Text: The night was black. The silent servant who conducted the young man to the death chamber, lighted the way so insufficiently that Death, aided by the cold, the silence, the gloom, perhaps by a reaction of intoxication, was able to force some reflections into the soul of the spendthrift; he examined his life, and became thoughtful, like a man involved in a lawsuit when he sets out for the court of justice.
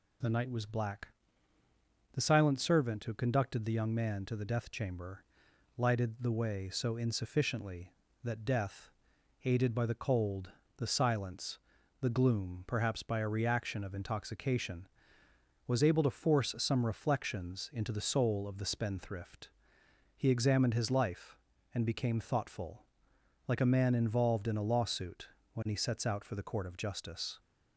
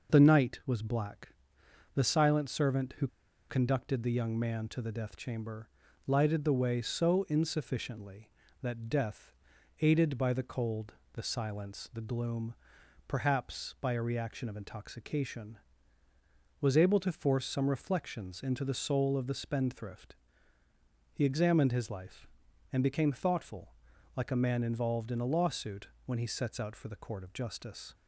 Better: first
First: pauses between "lawsuit" and "when"; slight; at 25.2 s; 0.24 s long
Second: pauses between "who" and "conducted"; at 3.0 s; 0.42 s long // pauses between "lawsuit" and "when"; slight; at 25.8 s; 0.20 s long

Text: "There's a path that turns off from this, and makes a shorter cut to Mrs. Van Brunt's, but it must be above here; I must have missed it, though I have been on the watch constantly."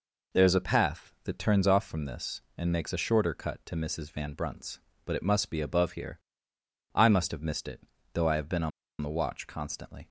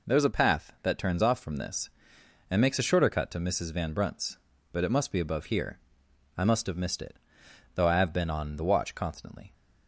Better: second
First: pauses between "on" and "the"; slight; at 8.7 s; 0.31 s long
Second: none

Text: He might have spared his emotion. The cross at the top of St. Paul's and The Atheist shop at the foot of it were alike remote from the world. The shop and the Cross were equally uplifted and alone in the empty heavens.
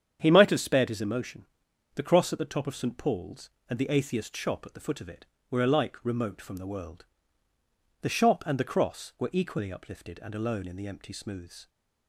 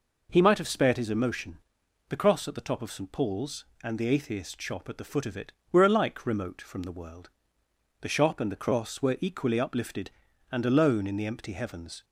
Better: second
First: starts louder than the rest; strong; until 1.2 s; 8 dB // says "smooths" for "heavens"; at 11.1 s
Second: none

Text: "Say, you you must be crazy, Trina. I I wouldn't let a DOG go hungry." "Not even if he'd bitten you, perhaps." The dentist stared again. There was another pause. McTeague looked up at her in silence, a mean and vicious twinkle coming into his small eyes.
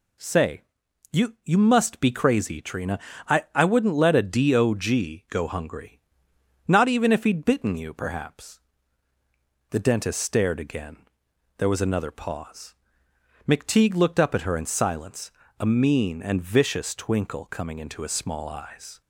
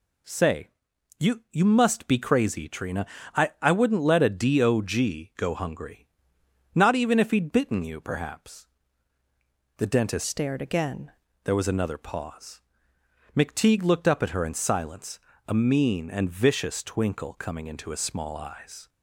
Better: first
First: none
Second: changes voice from "stared" to "again"; from 10.2 to 11.0 s; 0.8 s long

